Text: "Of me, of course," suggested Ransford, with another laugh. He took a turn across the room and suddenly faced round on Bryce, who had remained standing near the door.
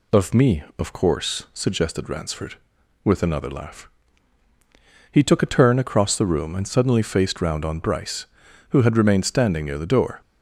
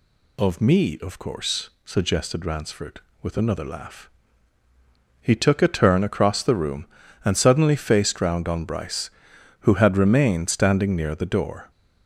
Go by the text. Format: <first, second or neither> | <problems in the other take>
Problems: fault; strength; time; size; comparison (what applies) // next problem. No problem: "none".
neither | none